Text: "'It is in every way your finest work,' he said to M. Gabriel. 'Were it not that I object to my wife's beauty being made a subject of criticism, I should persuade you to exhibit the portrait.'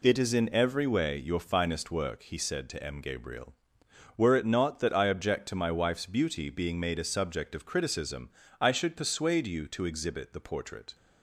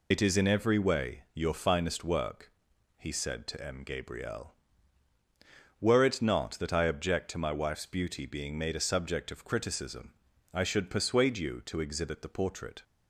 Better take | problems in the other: first | loses the start of "It"; at 0.1 s; 65 ms

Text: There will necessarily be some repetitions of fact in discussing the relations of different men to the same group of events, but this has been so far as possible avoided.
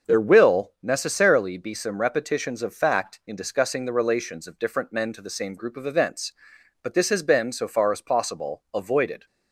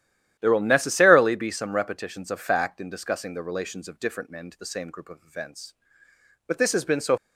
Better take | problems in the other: first | starts louder than the rest; strong; until 1.4 s; 11.5 dB; also in the first // stops before "far as possible avoided"; at 7.1 s

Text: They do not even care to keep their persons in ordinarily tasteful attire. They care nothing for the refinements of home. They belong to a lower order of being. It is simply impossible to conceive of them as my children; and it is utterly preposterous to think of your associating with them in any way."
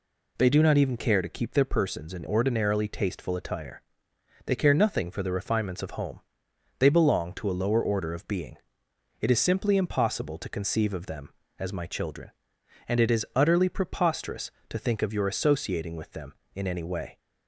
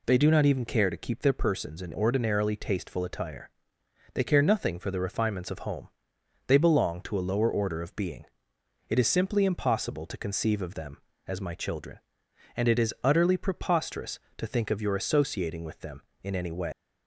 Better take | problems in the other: first | leaves "way" unfinished; at 16.7 s; 135 ms

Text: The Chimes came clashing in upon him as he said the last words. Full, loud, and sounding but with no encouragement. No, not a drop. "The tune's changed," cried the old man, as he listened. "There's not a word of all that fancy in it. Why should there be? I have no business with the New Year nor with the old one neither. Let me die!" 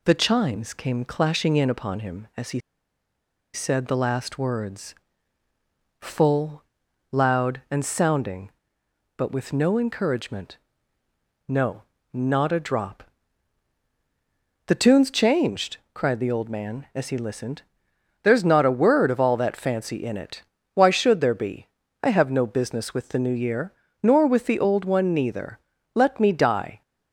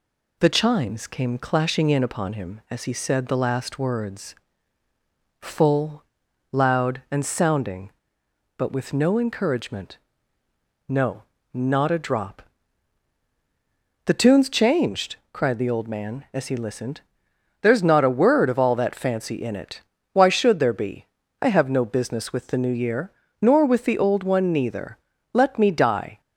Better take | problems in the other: second | pauses between "he" and "said"; noticeable; at 2.5 s; 0.95 s long // pauses between "Year" and "nor"; slight; at 23.7 s; 0.30 s long; slight in the second

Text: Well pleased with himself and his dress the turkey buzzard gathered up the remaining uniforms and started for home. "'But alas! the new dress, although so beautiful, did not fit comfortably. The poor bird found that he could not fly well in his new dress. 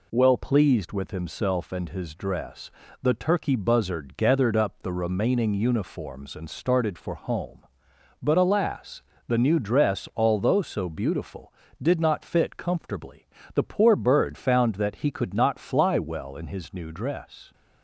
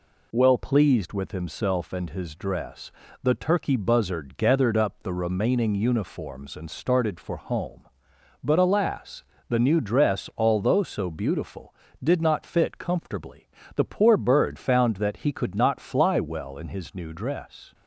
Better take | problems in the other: neither | pauses between "dress" and "the"; slight; the same in both

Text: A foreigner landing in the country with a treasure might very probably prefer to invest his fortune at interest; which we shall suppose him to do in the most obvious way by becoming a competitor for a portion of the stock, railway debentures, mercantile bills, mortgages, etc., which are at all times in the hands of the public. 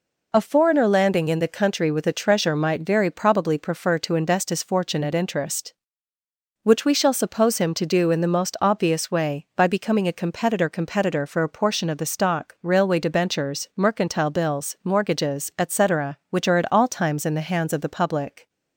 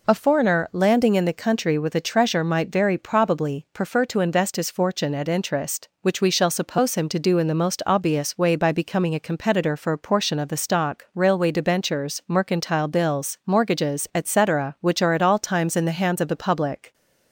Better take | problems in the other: second | says "competitor" twice; at 10.6 s

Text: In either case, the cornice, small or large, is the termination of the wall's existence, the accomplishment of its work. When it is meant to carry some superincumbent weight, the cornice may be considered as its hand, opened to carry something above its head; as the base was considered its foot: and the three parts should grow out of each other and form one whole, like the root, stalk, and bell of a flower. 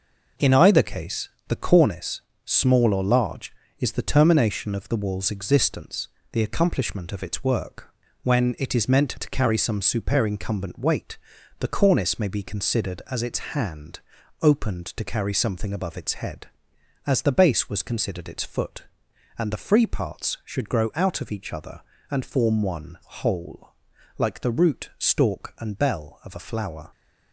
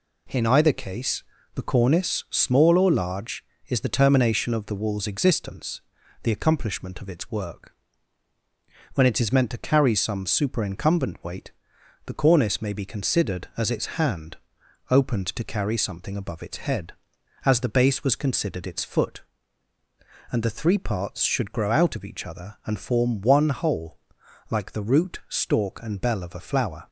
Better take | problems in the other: second | says "free" for "three"; at 19.6 s

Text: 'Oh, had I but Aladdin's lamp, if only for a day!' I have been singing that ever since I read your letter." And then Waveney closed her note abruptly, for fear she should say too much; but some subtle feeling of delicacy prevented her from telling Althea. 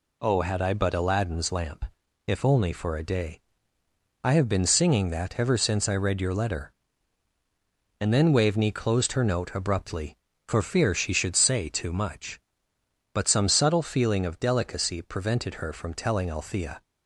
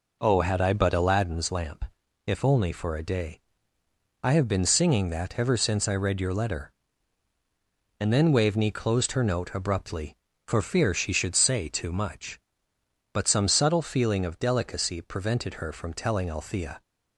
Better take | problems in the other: first | starts louder than the rest; noticeable; until 1.3 s; 4.5 dB

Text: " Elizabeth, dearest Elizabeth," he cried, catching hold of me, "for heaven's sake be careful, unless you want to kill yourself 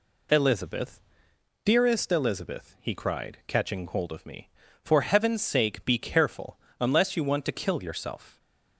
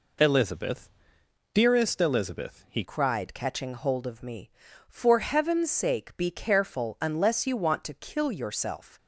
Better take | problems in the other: first | changes voice at "cried"; from 2.8 s on; 6.1 s long

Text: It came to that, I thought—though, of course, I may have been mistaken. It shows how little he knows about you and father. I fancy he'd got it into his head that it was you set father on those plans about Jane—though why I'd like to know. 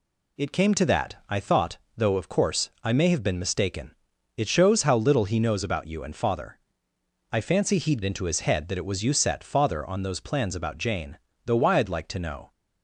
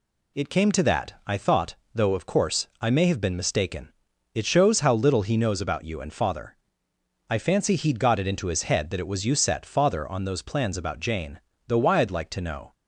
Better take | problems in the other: second | skips "got it"; at 8.0 s

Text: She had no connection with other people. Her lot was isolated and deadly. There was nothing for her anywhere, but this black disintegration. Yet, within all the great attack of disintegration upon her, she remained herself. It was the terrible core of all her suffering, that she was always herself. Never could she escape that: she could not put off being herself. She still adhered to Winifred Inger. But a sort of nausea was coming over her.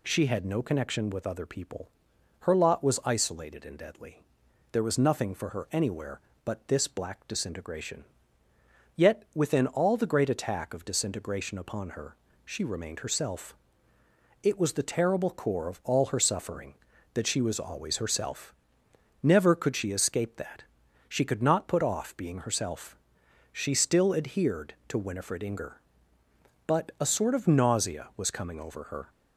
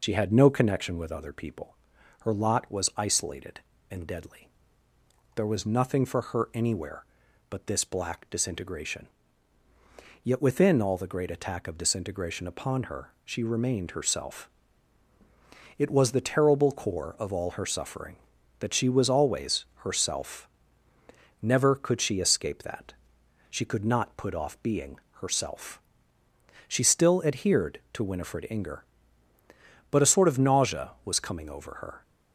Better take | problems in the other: first | loses the start of "She"; at 0.0 s; 50 ms // pauses between "being" and "herself"; slight; at 24.9 s; 0.22 s long

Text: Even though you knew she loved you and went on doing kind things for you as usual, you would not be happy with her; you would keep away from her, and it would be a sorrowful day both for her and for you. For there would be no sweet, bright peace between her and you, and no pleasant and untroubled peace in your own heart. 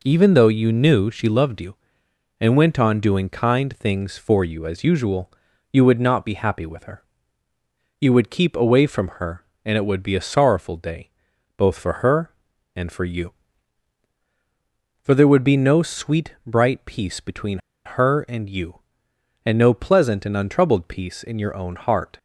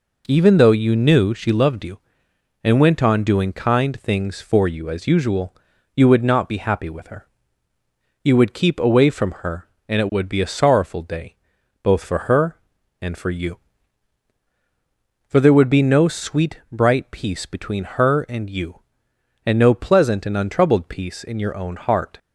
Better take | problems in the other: second | pauses between "day" and "both"; noticeable; at 11.0 s; 0.48 s long; noticeable in the second // pauses between "between" and "her"; slight; at 17.5 s; 0.27 s long

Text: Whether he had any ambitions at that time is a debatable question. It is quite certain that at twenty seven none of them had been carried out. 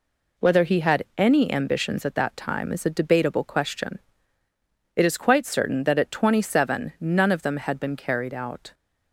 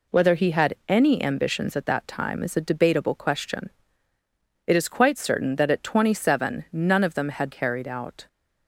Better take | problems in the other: first | skips "been"; at 7.5 s

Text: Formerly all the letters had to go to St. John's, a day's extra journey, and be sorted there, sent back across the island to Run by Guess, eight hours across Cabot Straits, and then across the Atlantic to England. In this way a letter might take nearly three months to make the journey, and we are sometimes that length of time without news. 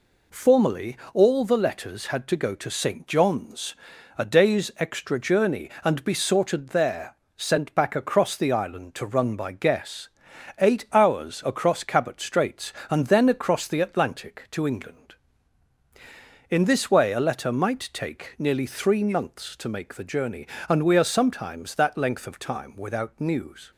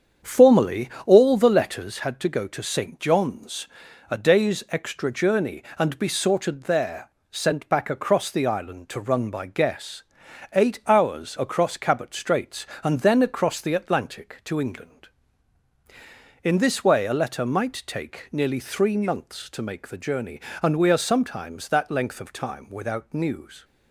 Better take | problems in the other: first | starts louder than the rest; strong; until 2.0 s; 7.5 dB // pauses between "Formerly" and "all"; slight; at 0.8 s; 0.16 s long; slight in the first

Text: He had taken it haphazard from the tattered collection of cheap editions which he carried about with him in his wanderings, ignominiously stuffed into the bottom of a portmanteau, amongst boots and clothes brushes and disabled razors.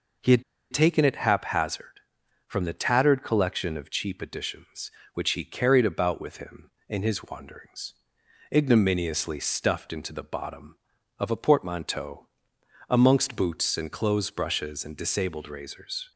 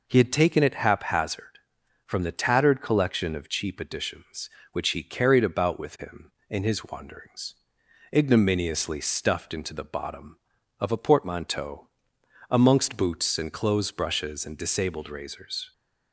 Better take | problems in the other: second | pauses between "had" and "taken"; slight; at 0.4 s; 0.30 s long

